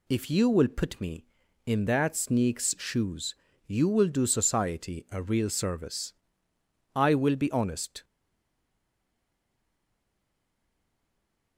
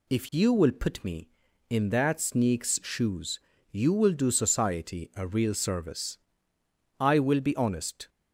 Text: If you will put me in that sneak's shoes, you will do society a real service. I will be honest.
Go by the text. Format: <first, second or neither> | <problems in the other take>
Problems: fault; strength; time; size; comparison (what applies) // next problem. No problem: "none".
second | stays silent after the last word; strong; from 8.0 s on; 3.5 s long